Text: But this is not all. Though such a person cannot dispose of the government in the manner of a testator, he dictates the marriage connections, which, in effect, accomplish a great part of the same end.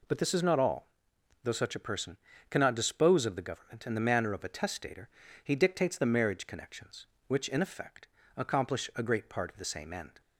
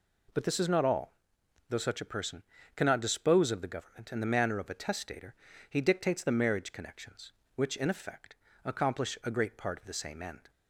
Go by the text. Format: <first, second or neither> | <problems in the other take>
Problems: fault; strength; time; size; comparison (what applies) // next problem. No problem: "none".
neither | pauses between "person" and "cannot"; slight; the same in both